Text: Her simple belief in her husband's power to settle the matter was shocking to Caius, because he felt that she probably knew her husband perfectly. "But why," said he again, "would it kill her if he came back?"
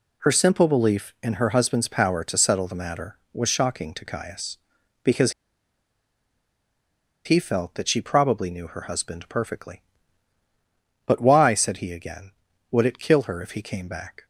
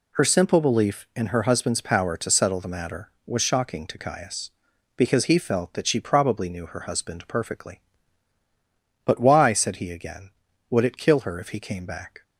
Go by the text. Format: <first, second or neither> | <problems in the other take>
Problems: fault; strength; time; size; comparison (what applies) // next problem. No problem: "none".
second | pauses between "because" and "he"; strong; at 5.3 s; 1.9 s long